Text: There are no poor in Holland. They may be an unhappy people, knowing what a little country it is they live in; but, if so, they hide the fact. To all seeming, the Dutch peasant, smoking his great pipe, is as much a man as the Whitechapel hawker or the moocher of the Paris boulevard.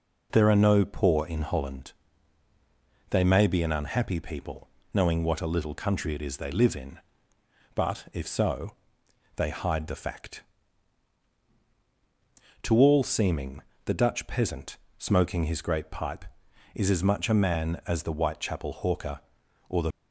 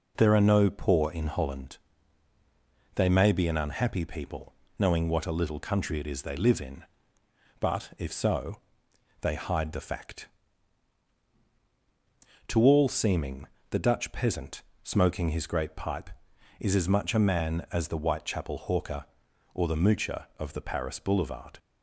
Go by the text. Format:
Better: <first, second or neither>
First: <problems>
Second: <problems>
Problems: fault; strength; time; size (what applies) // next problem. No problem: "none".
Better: second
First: stops before "moocher of the Paris boulevard"; at 19.9 s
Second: none